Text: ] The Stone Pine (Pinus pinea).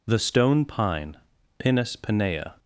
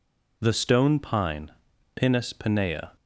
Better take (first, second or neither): neither